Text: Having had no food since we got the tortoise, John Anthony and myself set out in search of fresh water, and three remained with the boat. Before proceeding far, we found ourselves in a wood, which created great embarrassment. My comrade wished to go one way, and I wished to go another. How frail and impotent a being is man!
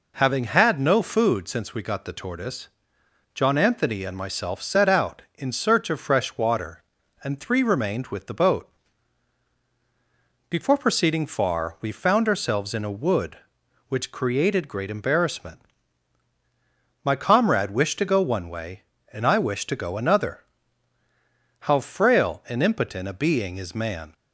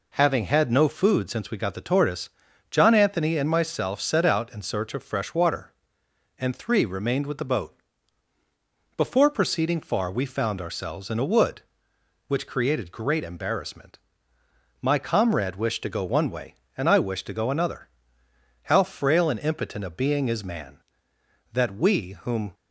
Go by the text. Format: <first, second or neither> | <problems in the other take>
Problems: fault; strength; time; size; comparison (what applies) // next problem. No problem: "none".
first | goes on to say "That we whom"; noticeable; from 21.5 s on; 1.0 s long